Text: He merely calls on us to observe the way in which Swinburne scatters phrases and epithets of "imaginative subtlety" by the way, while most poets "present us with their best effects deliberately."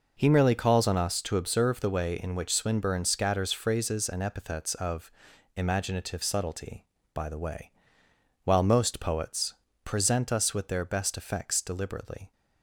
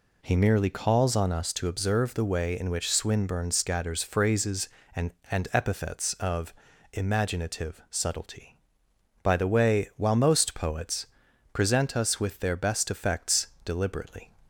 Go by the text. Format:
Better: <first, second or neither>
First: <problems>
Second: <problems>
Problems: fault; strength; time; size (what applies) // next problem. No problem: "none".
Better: first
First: pauses between "of" and "imaginative"; at 5.1 s; 0.44 s long // pauses between "poets" and "present"; slight; at 9.5 s; 0.30 s long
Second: says "and" twice; at 5.3 s // pauses between "of" and "imaginative"; at 6.5 s; 0.40 s long // pauses between "poets" and "present"; noticeable; at 11.0 s; 0.46 s long // pauses between "effects" and "deliberately"; slight; at 13.4 s; 0.18 s long